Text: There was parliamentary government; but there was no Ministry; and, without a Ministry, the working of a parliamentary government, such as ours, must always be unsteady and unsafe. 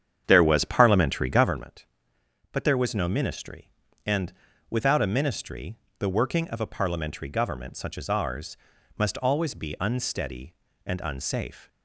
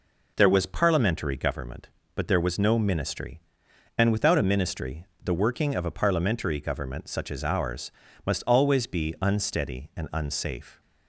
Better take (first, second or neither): second